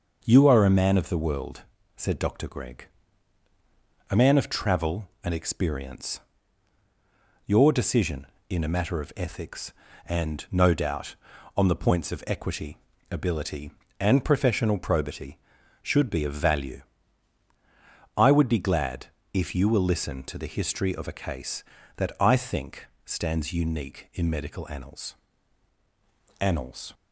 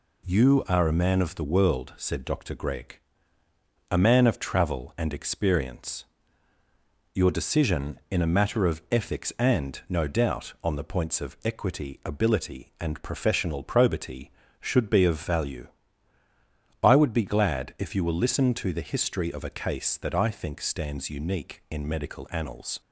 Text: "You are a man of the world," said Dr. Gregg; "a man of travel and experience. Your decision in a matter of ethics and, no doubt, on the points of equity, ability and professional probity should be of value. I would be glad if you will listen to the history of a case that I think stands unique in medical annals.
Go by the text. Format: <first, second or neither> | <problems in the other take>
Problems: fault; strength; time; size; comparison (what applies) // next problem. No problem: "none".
second | starts louder than the rest; noticeable; until 1.2 s; 6 dB // pauses between "glad" and "if"; slight; at 19.0 s; 0.26 s long // pauses between "think" and "stands"; slight; at 22.8 s; 0.20 s long // says "annals" twice; at 26.3 s